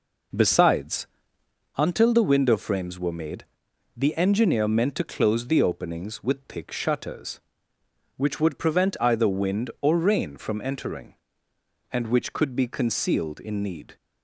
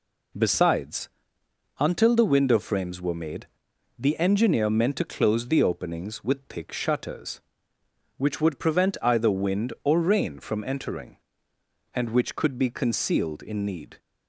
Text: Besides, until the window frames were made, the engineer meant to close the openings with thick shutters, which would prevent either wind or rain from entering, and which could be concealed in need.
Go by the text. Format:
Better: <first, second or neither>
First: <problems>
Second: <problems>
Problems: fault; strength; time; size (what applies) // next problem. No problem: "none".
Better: second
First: starts louder than the rest; noticeable; until 1.7 s; 5 dB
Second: none